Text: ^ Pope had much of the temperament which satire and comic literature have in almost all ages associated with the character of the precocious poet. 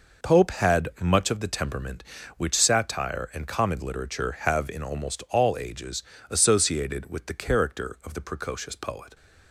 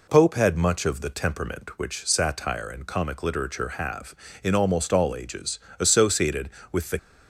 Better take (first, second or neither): first